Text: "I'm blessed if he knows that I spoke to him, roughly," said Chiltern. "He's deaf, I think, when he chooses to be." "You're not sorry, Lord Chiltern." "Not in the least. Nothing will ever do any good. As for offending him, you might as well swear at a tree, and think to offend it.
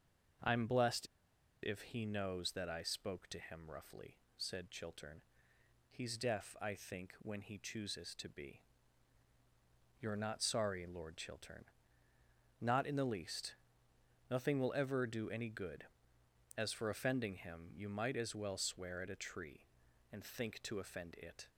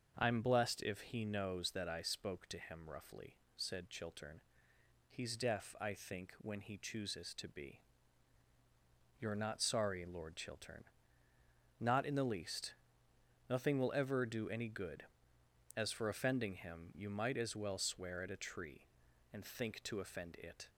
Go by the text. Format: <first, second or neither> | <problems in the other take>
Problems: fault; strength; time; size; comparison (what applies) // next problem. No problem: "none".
second | starts louder than the rest; until 1.9 s; 6.5 dB; also in the second // pauses between "blessed" and "if"; noticeable; at 1.0 s; 0.55 s long